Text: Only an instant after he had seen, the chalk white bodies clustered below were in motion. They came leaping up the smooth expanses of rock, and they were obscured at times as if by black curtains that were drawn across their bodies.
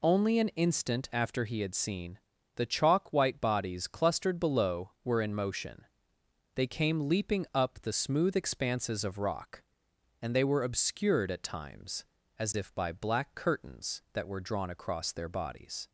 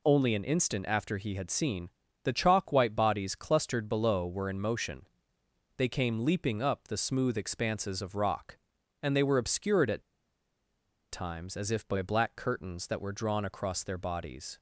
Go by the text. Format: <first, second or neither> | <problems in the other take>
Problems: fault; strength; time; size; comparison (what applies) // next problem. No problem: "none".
first | pauses between "at" and "times"; at 10.0 s; 1.0 s long